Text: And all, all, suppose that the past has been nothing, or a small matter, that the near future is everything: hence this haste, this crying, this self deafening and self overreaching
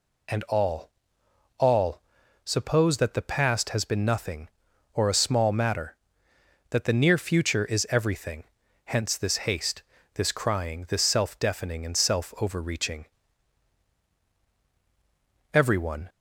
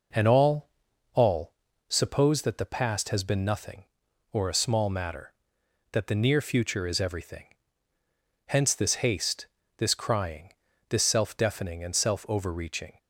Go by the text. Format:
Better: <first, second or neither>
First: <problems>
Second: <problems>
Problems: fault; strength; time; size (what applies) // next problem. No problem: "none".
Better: second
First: goes on to say "Everyone"; from 15.5 s on; 0.56 s long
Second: none